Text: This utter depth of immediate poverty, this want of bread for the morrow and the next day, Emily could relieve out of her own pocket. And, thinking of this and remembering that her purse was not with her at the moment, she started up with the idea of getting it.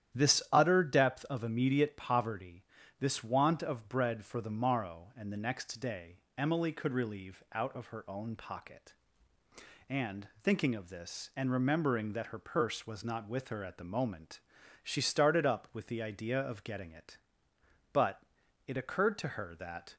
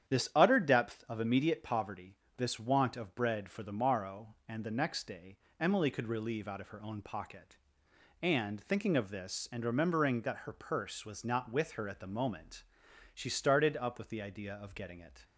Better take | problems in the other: second | starts louder than the rest; strong; until 1.2 s; 10.5 dB; strong in the second // goes on to say "But it occurred to her that"; strong; from 17.9 s on; 2.0 s long

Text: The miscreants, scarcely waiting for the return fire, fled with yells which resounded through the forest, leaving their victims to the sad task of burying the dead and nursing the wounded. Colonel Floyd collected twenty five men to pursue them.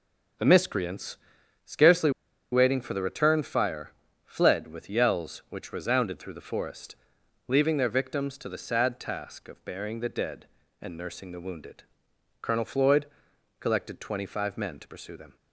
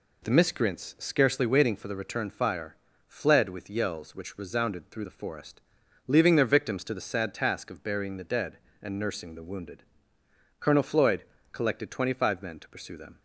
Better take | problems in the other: second | pauses between "scarcely" and "waiting"; at 2.1 s; 0.41 s long // pauses between "Floyd" and "collected"; noticeable; at 13.0 s; 0.54 s long; slight in the second

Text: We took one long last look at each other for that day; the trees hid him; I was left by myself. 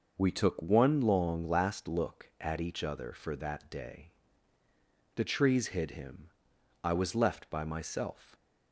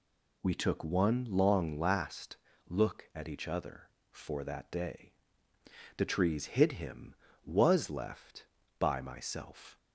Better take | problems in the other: first | pauses between "last" and "look"; slight; at 2.3 s; 0.32 s long // skips "I"; at 7.2 s

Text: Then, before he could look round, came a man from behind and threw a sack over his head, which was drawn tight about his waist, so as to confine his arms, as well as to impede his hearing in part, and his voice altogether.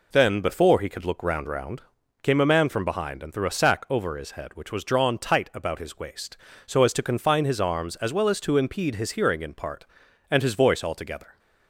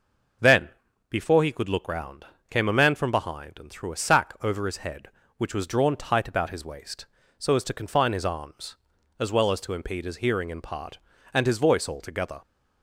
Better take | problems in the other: second | says "round" twice; at 1.4 s

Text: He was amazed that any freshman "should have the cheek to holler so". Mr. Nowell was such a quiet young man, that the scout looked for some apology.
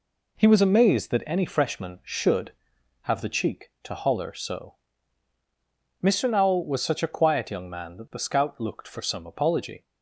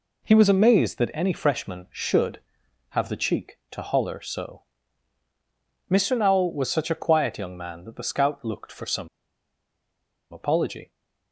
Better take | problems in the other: first | pauses between "some" and "apology"; strong; at 9.0 s; 1.2 s long

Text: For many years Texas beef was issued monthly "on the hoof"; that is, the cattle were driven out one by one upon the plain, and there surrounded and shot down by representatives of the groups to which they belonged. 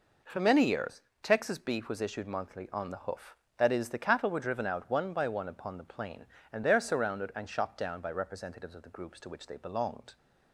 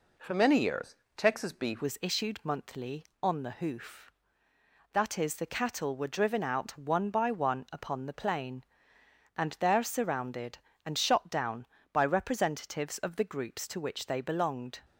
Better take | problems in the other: first | pauses between "years" and "Texas"; slight; at 0.9 s; 0.22 s long; slight in the first // changes voice at "was"; from 1.8 s on; 13.0 s long

